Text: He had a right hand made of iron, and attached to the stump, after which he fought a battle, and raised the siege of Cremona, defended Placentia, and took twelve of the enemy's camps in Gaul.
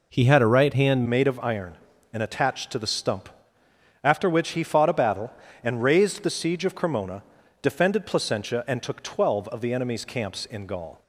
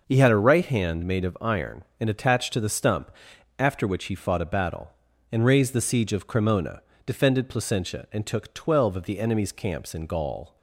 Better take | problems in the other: second | changes voice at "made"; from 1.0 s on; 10.0 s long

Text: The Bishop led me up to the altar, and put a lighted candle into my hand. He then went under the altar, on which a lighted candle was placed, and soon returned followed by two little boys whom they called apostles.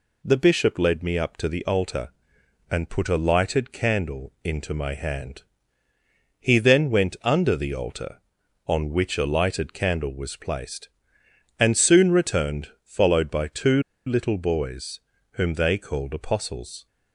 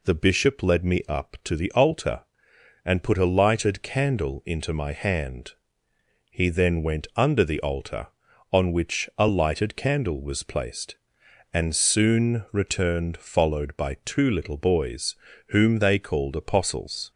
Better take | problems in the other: second | pauses between "returned" and "followed"; slight; at 12.6 s; 0.16 s long // pauses between "two" and "little"; slight; at 13.8 s; 0.24 s long // pauses between "boys" and "whom"; slight; at 14.9 s; 0.34 s long; slight in the second

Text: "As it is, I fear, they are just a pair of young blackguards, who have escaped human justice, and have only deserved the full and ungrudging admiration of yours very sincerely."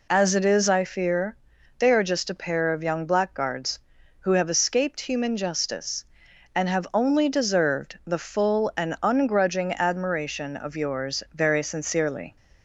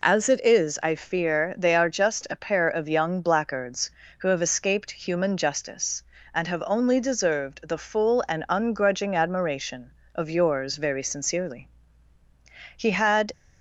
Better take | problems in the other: first | goes on to say "He had"; from 12.7 s on; 0.56 s long

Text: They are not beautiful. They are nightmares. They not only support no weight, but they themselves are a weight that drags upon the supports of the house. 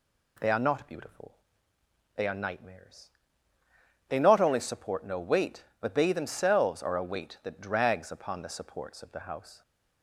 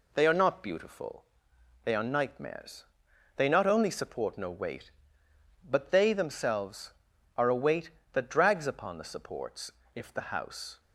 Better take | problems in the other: first | says "if" for "of"; at 9.9 s

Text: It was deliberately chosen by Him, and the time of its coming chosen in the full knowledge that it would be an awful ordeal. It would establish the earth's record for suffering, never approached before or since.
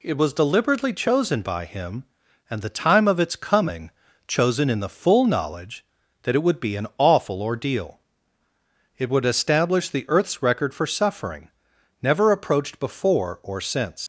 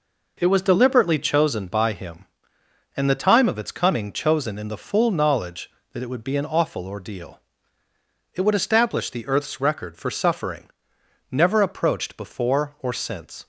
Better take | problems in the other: second | pauses between "coming" and "chosen"; slight; at 3.9 s; 0.36 s long // leaves "since" unfinished; at 14.0 s; 100 ms

